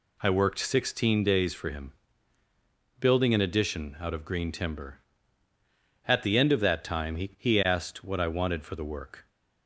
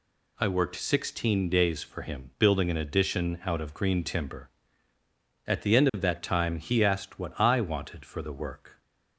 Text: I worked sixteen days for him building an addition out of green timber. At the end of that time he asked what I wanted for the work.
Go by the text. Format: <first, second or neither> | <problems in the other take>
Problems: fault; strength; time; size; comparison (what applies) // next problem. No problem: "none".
second | pauses between "him" and "building"; at 1.9 s; 1.0 s long // says "he" twice; at 7.3 s